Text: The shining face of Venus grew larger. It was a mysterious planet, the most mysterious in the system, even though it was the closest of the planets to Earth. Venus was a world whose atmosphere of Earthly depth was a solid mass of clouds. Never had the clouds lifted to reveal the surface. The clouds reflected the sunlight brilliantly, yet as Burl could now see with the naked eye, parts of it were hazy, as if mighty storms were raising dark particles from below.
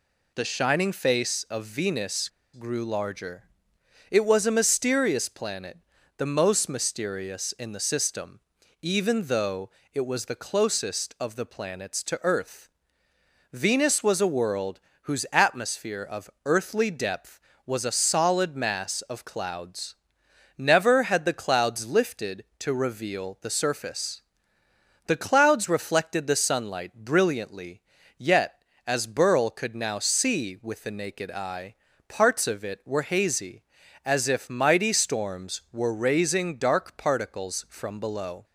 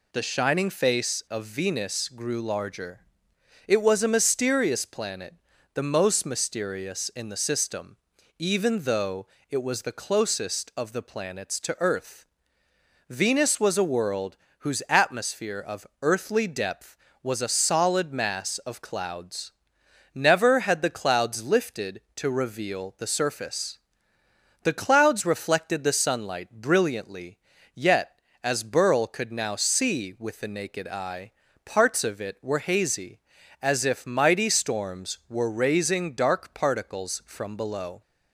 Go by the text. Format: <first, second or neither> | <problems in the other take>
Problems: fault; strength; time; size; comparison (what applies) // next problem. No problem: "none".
second | pauses between "Venus" and "grew"; slight; at 2.2 s; 0.24 s long // pauses between "though" and "it"; slight; at 9.6 s; 0.24 s long; slight in the second // pauses between "world" and "whose"; slight; at 14.7 s; 0.24 s long; slight in the second